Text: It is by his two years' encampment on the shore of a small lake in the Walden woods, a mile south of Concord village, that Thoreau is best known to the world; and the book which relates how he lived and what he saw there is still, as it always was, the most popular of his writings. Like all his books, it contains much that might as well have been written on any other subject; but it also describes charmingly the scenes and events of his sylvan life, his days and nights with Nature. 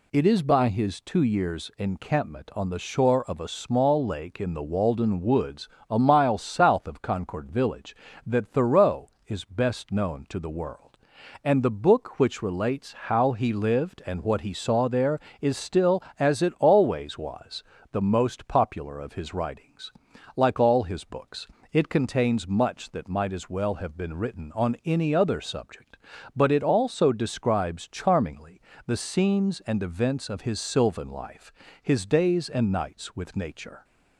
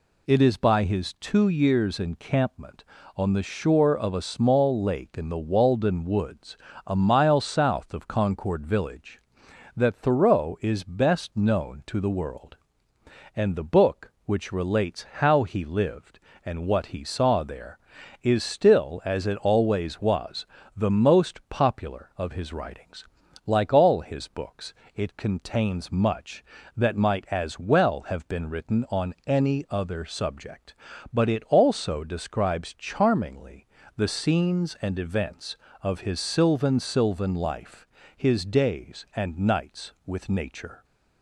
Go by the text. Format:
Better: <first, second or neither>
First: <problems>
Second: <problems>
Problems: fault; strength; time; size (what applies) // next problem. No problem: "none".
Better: first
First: pauses between "charmingly" and "the"; slight; at 28.5 s; 0.30 s long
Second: pauses between "charmingly" and "the"; slight; at 33.6 s; 0.30 s long // says "sylvan" twice; at 36.7 s